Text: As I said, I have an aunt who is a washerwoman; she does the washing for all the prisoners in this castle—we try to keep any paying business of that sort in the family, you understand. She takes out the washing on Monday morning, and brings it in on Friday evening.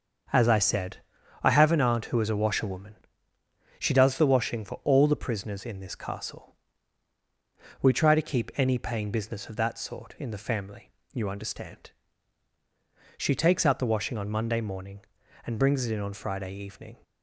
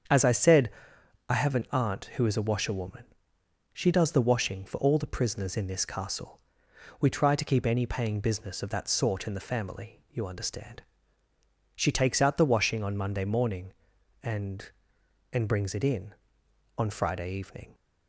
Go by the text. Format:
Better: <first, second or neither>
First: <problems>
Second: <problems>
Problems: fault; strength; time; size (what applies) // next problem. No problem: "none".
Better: first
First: starts louder than the rest; until 1.7 s; 7 dB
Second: starts louder than the rest; strong; until 1.6 s; 7.5 dB // says "and" twice; at 15.3 s